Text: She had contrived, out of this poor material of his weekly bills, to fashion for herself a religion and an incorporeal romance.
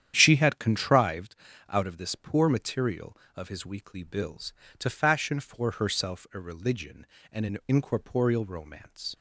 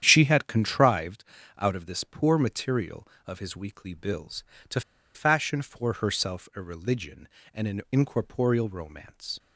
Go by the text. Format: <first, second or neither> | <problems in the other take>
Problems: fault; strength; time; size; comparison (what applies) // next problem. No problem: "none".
first | starts louder than the rest; strong; until 1.0 s; 10 dB; strong in the first // pauses between "to" and "fashion"; slight; at 4.8 s; 0.33 s long